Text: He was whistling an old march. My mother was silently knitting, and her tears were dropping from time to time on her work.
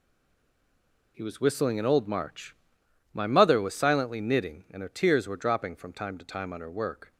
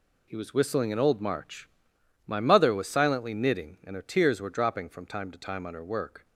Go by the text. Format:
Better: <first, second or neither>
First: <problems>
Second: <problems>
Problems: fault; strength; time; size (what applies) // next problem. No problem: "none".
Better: second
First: stays silent before the first word; until 1.1 s; 1.1 s long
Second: none